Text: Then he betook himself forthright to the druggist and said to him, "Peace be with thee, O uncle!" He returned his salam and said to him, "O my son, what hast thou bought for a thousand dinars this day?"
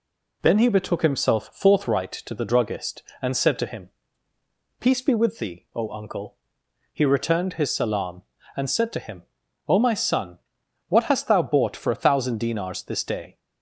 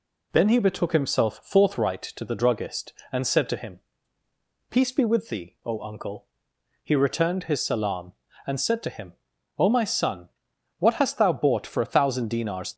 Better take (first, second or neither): first